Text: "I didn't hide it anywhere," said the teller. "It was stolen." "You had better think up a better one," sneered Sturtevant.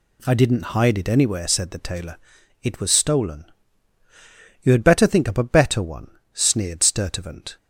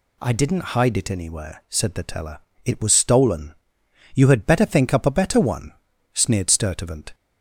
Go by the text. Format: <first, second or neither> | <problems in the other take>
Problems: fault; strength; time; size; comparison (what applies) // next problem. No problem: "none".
second | says "tailor" for "teller"; at 1.7 s